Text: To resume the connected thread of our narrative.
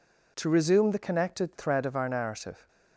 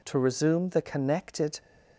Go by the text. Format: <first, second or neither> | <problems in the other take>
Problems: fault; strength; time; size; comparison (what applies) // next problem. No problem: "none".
first | stops before "thread of our narrative"; at 1.6 s